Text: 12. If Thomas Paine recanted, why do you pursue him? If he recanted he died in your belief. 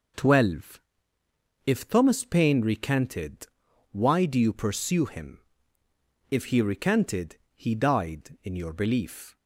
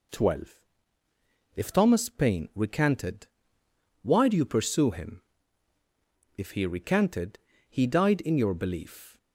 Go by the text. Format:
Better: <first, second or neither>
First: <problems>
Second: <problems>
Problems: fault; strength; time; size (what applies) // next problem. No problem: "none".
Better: neither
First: pauses between "recanted" and "he"; slight; at 7.3 s; 0.20 s long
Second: pauses between "recanted" and "he"; slight; at 7.3 s; 0.30 s long